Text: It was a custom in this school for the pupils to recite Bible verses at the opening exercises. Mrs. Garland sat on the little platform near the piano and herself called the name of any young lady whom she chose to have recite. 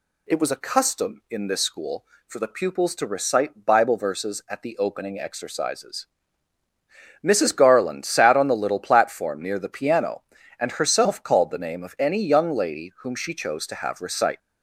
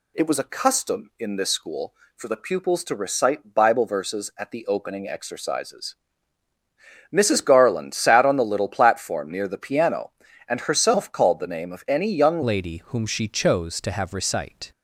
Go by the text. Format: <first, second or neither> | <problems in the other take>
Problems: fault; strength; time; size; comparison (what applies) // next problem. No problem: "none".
first | changes voice at "lady"; from 12.4 s on; 2.3 s long